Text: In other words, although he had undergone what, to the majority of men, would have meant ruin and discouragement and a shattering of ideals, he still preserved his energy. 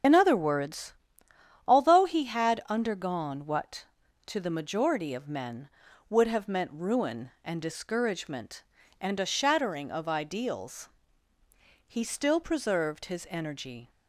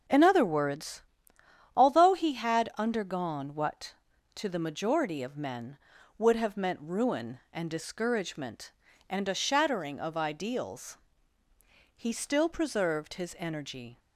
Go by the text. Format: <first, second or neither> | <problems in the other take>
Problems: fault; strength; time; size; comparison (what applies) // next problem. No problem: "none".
second | loses the start of "In"; at 0.0 s; 45 ms // starts louder than the rest; strong; until 1.7 s; 7.5 dB; also in the second